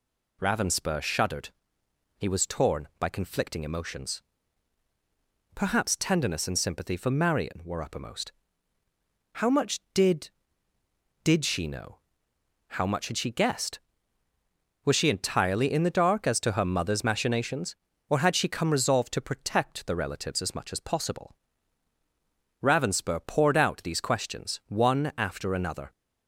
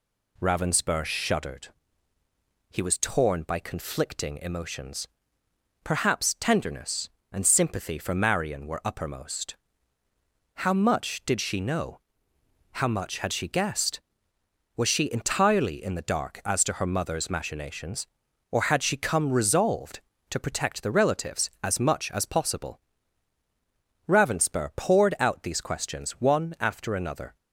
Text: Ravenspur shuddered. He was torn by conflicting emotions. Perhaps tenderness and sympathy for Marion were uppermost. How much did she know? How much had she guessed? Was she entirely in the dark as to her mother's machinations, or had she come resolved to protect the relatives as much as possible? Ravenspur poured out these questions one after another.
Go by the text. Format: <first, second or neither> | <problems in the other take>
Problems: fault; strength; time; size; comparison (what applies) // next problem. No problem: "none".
second | says "did" twice; at 11.2 s